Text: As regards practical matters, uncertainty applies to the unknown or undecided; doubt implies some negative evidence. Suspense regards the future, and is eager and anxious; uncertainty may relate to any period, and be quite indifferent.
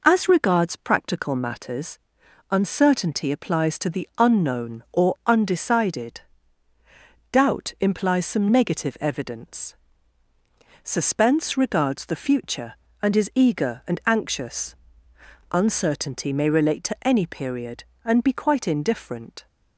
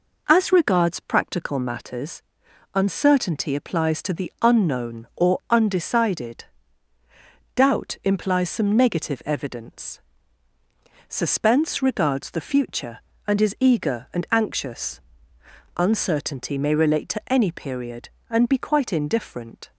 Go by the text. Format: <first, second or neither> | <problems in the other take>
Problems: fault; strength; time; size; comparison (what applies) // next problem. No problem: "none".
neither | none